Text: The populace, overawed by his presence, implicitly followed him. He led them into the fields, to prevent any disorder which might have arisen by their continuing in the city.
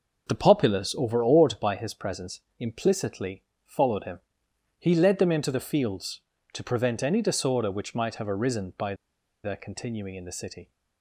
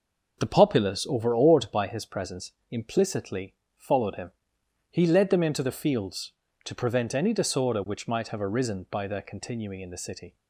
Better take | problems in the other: second | pauses between "implicitly" and "followed"; slight; at 3.4 s; 0.22 s long; slight in the second // pauses between "by" and "their"; noticeable; at 8.9 s; 0.49 s long

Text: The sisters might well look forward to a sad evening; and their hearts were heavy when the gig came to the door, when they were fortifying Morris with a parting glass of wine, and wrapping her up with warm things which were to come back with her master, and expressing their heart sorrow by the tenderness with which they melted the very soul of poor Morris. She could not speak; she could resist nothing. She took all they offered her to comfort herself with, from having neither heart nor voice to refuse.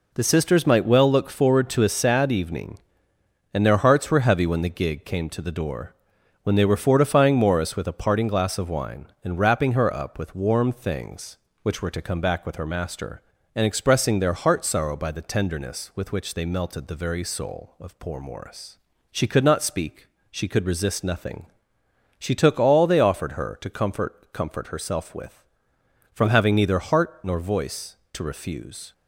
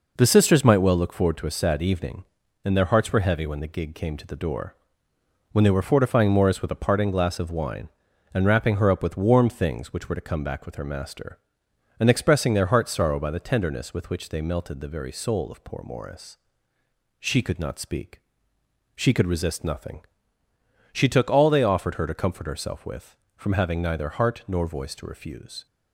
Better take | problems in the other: second | says "comfort" twice; at 24.3 s

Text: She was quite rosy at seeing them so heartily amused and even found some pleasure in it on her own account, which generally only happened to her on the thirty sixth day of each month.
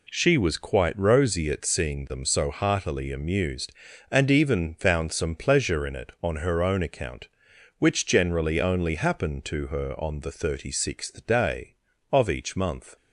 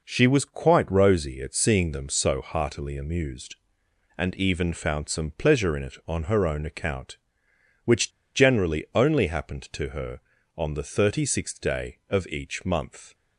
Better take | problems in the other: first | pauses between "which" and "generally"; slight; at 8.1 s; 0.23 s long

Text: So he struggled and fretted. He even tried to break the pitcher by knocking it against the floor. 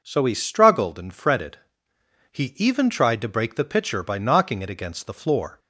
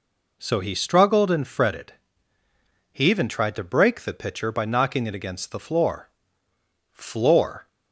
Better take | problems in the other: first | says "floor" twice; at 6.9 s

